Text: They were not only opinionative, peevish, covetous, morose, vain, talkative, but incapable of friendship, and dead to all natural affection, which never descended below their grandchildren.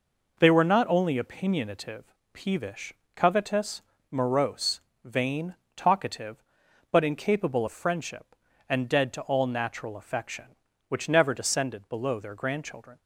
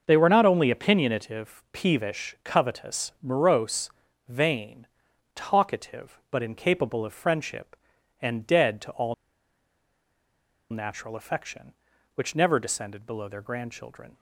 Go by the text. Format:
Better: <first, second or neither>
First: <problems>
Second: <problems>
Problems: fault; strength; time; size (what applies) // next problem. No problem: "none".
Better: first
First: none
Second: starts louder than the rest; until 1.0 s; 6 dB // pauses between "all" and "natural"; strong; at 9.1 s; 1.5 s long